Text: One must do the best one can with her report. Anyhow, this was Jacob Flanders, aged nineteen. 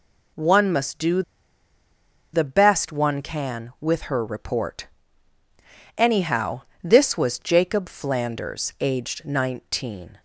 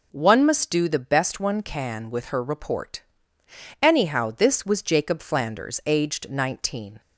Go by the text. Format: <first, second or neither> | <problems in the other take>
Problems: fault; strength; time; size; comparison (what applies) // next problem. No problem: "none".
second | pauses between "do" and "the"; at 1.2 s; 1.1 s long